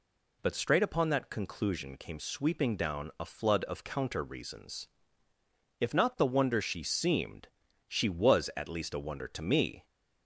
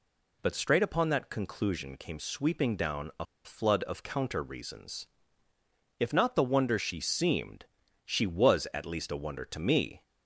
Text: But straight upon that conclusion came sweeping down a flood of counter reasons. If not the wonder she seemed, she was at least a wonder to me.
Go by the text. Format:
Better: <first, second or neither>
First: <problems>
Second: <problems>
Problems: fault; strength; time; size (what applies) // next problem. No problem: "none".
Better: first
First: none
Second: pauses between "a" and "flood"; slight; at 3.2 s; 0.19 s long